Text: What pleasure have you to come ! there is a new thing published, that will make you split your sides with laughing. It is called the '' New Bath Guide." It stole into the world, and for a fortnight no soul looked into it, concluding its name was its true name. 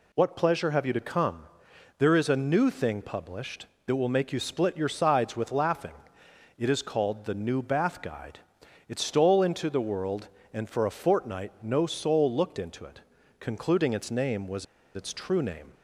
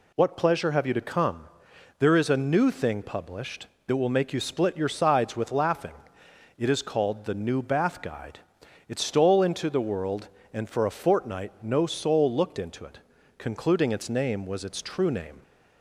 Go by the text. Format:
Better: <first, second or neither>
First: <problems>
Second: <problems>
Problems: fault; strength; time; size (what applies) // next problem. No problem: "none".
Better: second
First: pauses between "was" and "its"; slight; at 14.6 s; 0.30 s long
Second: none